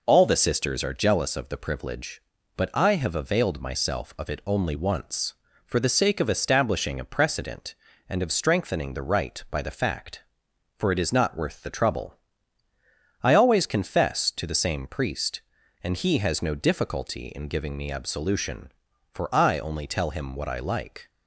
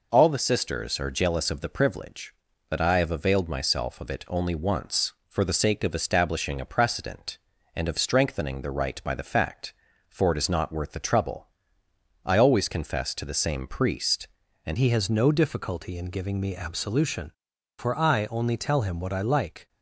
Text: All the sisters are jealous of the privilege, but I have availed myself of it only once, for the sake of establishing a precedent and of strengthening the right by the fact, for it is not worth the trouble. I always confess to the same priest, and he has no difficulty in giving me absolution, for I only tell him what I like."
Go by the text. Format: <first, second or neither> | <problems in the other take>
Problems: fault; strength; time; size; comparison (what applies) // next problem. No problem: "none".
first | changes voice at "he"; from 14.7 s on; 4.9 s long